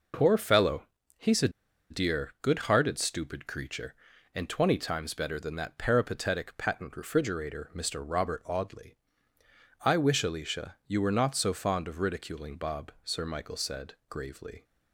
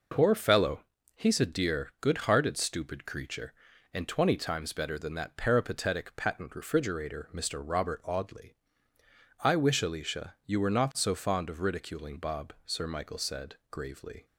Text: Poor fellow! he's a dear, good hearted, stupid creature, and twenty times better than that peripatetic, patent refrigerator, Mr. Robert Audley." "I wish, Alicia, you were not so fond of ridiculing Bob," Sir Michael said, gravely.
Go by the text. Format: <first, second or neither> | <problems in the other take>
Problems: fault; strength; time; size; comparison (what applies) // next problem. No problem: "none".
second | pauses between "a" and "dear"; at 1.4 s; 0.41 s long